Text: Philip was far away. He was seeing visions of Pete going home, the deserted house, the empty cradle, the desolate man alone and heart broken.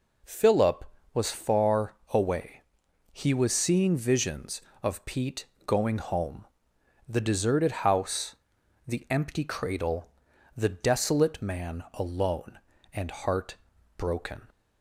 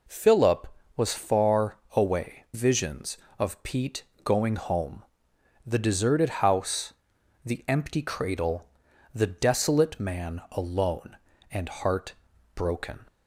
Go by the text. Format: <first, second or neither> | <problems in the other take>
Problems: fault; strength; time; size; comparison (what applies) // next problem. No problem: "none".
first | pauses between "far" and "away"; slight; at 1.7 s; 0.18 s long; slight in the first // skips "He was seeing"; at 2.4 s // pauses between "Pete" and "going"; slight; at 4.0 s; 0.22 s long; slight in the first // pauses between "heart" and "broken"; at 12.1 s; 0.40 s long; also in the first